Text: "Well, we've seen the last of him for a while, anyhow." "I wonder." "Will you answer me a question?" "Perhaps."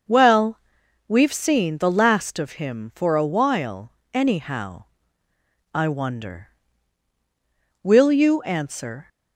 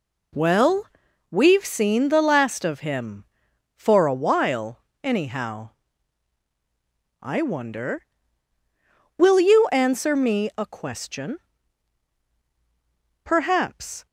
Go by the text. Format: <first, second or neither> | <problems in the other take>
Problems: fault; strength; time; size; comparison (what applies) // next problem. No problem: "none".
second | starts louder than the rest; until 1.5 s; 6.5 dB // stops before "me a question Perhaps"; at 9.0 s